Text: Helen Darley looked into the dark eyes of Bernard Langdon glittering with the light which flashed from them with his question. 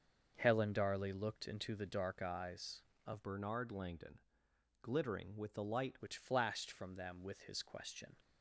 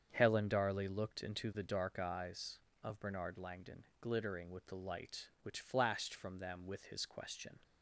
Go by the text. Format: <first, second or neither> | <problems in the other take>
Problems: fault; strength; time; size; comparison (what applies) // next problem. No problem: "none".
second | starts louder than the rest; until 1.3 s; 6.5 dB; strong in the second // changes voice from "Bernard" to "light"; from 3.2 to 5.9 s; 2.7 s long // pauses between "Langdon" and "glittering"; noticeable; at 4.2 s; 0.60 s long; slight in the second